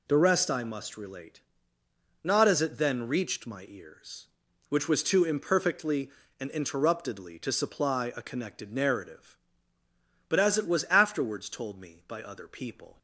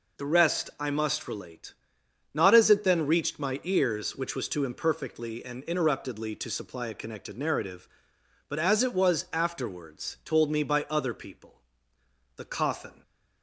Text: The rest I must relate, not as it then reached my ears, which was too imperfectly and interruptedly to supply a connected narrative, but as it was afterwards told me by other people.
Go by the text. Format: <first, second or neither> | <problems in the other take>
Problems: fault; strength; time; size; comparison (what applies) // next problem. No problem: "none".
first | goes on to say "The coffin"; noticeable; from 12.3 s on; 0.66 s long